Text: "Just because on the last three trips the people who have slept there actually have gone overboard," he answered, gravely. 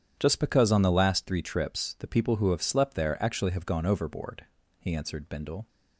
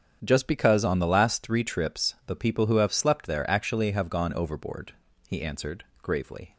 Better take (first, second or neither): second